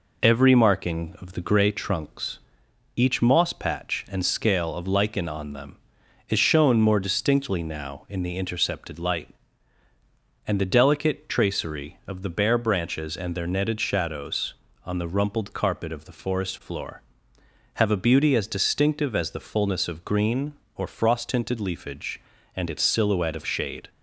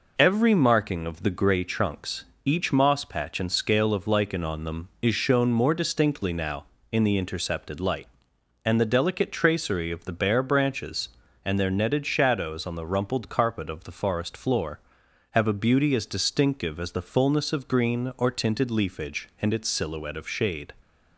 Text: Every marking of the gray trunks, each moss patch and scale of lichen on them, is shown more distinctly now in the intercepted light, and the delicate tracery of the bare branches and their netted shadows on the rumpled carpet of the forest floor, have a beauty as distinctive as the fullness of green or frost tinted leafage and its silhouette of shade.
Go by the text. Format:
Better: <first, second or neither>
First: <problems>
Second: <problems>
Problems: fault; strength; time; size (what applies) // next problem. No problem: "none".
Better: first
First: none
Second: skips "frost"; at 18.3 s